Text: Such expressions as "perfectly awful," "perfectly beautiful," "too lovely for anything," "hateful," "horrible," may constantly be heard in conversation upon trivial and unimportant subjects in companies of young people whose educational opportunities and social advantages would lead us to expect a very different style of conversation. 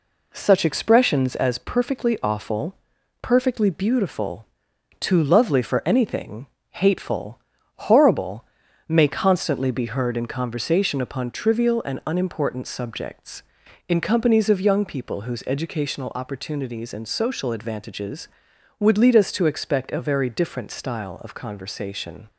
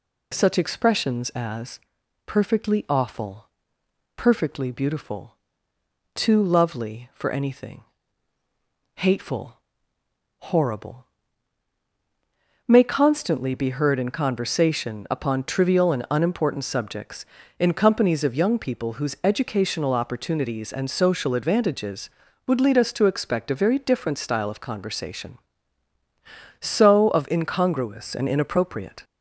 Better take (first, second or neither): first